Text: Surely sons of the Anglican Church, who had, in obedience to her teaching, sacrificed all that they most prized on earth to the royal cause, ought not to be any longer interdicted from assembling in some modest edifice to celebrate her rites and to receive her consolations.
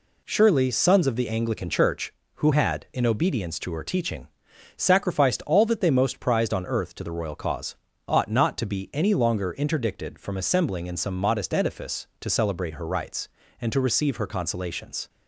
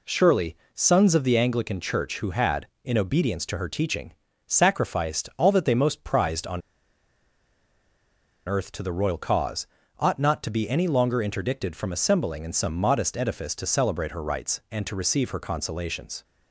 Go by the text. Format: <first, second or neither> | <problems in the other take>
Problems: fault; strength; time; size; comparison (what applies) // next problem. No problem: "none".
first | pauses between "Surely" and "sons"; slight; at 0.5 s; 0.20 s long // pauses between "on" and "earth"; strong; at 6.6 s; 1.8 s long